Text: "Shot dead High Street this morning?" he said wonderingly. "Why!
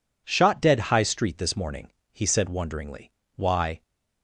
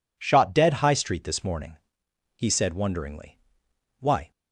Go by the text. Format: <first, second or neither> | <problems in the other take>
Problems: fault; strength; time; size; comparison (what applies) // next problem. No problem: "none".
neither | none